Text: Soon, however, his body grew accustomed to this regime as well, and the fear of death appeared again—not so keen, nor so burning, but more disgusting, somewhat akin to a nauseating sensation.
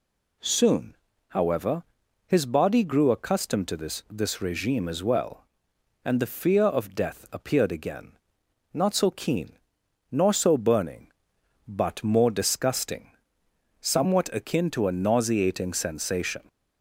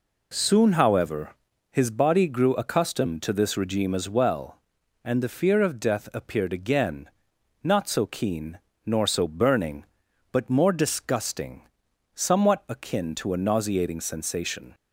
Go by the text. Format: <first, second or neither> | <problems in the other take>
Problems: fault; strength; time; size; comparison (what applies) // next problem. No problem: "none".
second | says "this" twice; at 4.1 s